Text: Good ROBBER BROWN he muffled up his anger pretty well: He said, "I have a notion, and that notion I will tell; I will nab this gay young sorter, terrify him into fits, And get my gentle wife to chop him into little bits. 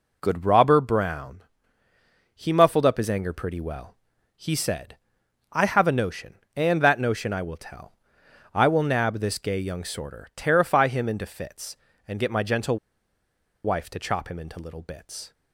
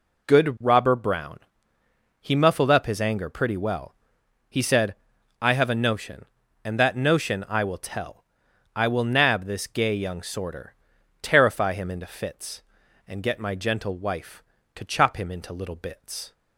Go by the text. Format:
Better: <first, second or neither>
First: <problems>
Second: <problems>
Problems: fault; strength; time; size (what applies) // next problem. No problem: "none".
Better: second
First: pauses between "BROWN" and "he"; noticeable; at 1.4 s; 0.92 s long // pauses between "gentle" and "wife"; noticeable; at 12.7 s; 0.88 s long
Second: pauses between "BROWN" and "he"; noticeable; at 1.3 s; 0.80 s long